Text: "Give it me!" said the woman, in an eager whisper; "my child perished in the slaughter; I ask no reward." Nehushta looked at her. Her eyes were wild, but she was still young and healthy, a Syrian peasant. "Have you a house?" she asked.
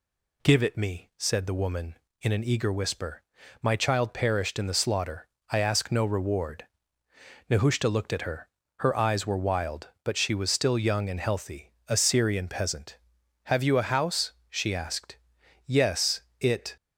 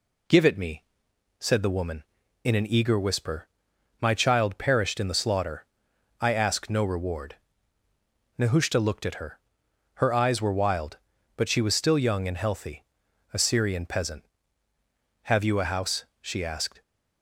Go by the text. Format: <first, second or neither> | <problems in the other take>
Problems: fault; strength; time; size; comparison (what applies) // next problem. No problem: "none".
second | goes on to say "Yes it"; noticeable; from 15.6 s on; 1.1 s long